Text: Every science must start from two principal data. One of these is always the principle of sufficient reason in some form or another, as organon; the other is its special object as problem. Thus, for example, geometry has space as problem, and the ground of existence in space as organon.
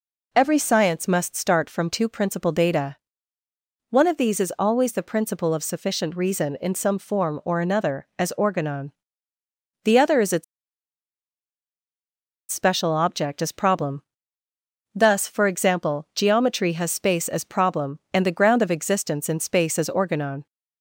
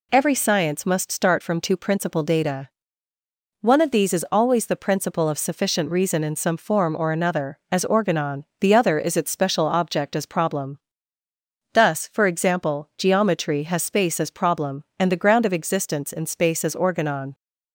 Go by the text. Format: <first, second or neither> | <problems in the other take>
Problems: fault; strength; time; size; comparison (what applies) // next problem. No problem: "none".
second | pauses between "its" and "special"; strong; at 10.4 s; 2.0 s long